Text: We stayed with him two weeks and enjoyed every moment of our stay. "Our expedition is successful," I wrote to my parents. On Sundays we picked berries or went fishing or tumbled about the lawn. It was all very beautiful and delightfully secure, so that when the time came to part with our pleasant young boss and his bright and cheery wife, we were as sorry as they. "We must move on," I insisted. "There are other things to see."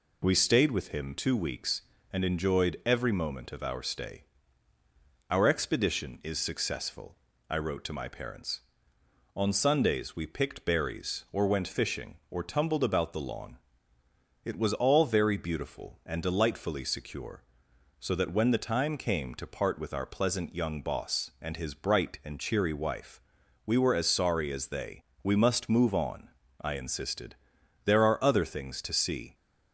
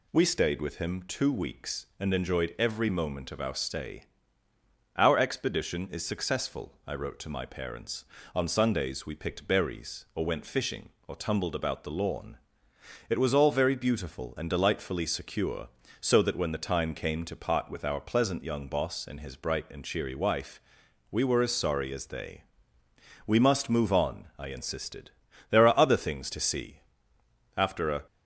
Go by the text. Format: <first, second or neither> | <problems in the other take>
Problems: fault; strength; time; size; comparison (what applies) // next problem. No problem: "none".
first | goes on to say "After a"; slight; from 27.5 s on; 0.48 s long